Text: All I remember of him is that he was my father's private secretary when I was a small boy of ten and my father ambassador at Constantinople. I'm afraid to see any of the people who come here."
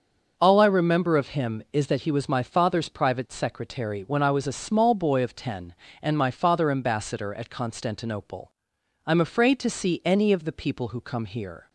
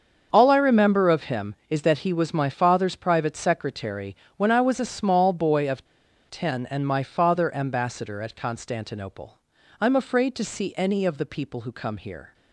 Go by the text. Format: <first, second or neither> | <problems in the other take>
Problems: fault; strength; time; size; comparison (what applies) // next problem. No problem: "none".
first | starts louder than the rest; until 1.3 s; 7 dB; also in the first // pauses between "secretary" and "when"; slight; at 4.1 s; 0.22 s long // pauses between "of" and "ten"; noticeable; at 5.8 s; 0.47 s long